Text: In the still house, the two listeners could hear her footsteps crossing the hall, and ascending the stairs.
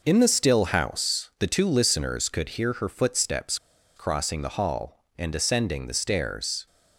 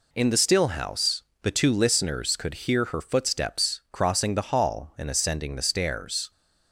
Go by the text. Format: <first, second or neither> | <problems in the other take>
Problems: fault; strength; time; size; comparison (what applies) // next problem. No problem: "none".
second | pauses between "footsteps" and "crossing"; at 3.5 s; 0.39 s long